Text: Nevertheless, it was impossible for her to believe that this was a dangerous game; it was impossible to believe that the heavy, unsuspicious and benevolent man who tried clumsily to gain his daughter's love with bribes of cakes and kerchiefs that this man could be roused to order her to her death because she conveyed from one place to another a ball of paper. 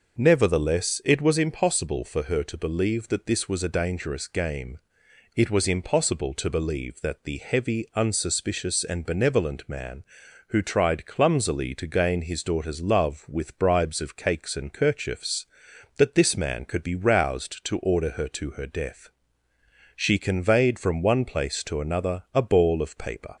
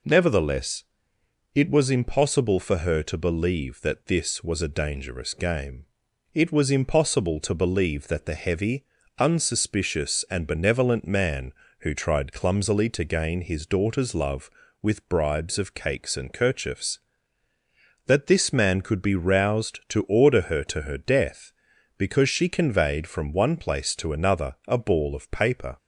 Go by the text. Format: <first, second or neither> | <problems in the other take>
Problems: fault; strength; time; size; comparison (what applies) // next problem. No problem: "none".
second | skips "because"; at 19.5 s